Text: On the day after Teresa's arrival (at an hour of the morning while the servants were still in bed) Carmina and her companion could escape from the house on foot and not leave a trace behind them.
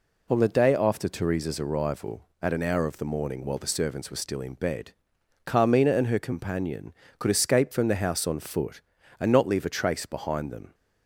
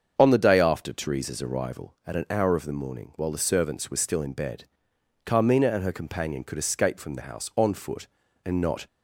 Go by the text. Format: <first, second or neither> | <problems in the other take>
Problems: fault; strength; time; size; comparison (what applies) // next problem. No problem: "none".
first | starts louder than the rest; until 1.1 s; 7 dB // stops before "leave a trace behind them"; at 8.8 s